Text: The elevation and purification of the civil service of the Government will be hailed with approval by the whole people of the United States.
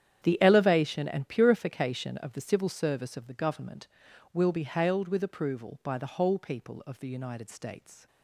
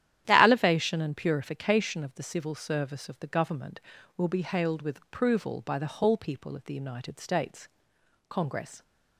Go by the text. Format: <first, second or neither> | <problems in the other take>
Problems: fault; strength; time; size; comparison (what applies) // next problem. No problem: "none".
first | starts louder than the rest; strong; until 1.2 s; 11 dB; strong in the first // goes on to say "Congress"; from 8.2 s on; 0.54 s long